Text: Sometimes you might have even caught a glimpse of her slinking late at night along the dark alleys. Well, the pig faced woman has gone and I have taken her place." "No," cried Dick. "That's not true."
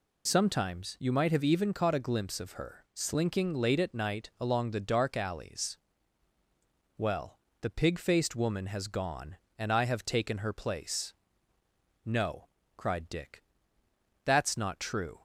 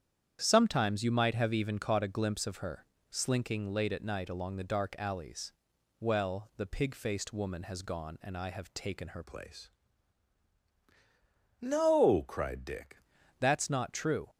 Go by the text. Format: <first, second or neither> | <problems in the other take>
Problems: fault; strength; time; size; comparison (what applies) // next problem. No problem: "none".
first | starts louder than the rest; strong; until 1.4 s; 9 dB // pauses between "her" and "slinking"; slight; at 2.8 s; 0.24 s long // changes voice from "place" to "Dick"; from 9.2 to 12.9 s; 3.7 s long